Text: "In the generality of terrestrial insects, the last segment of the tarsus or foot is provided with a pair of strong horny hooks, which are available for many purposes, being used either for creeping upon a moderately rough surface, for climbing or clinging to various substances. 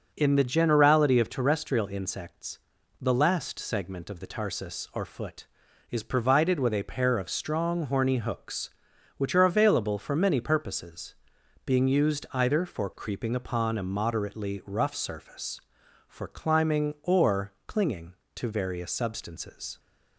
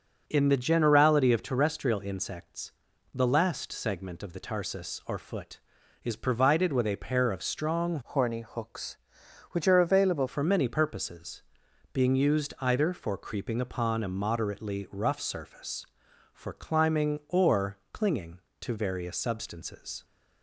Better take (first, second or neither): first